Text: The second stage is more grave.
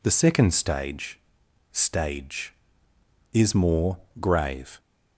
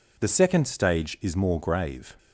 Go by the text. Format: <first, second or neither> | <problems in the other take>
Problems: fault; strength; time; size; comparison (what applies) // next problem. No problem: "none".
second | says "stage" twice; at 1.7 s // pauses between "more" and "grave"; slight; at 3.9 s; 0.24 s long